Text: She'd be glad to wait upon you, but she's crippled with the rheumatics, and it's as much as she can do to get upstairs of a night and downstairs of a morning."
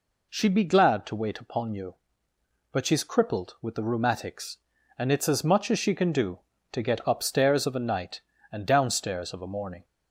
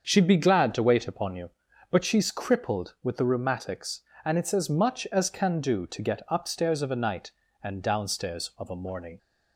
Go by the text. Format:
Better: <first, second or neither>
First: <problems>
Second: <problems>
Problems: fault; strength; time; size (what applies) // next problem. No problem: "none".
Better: first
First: none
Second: starts louder than the rest; until 1.1 s; 7 dB // skips "she"; at 5.2 s